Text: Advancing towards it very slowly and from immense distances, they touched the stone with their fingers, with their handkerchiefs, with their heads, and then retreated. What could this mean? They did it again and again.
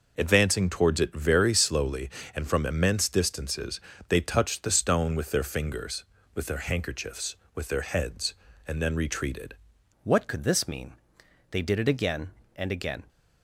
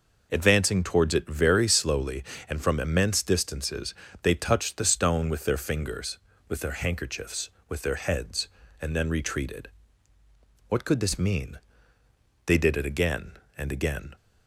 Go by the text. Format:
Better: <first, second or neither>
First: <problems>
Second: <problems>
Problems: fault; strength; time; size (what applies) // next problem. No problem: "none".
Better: second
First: changes voice at "What"; from 10.0 s on; 3.0 s long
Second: none